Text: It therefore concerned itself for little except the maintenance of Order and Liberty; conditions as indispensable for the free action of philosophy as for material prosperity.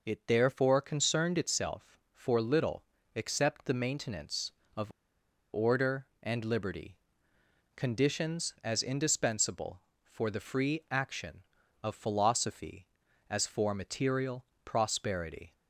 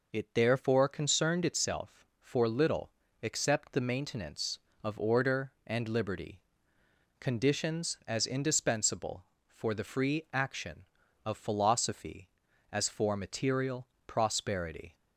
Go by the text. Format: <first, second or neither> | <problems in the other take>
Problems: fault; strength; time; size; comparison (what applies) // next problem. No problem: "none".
second | pauses between "little" and "except"; slight; at 2.8 s; 0.32 s long; slight in the second // pauses between "of" and "Order"; noticeable; at 4.9 s; 0.62 s long // pauses between "material" and "prosperity"; slight; at 14.4 s; 0.20 s long; slight in the second